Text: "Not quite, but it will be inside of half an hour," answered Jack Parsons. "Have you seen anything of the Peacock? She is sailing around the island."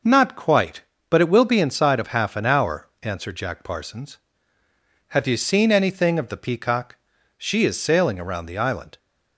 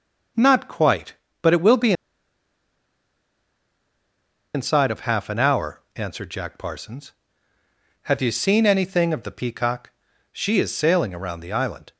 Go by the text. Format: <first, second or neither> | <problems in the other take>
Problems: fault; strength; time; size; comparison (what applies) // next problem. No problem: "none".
first | pauses between "be" and "inside"; strong; at 1.9 s; 2.6 s long